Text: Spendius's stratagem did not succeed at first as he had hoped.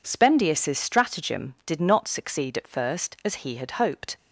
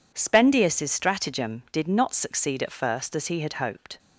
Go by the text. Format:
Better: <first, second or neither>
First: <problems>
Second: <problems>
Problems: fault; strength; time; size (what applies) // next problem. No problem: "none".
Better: neither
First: none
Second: none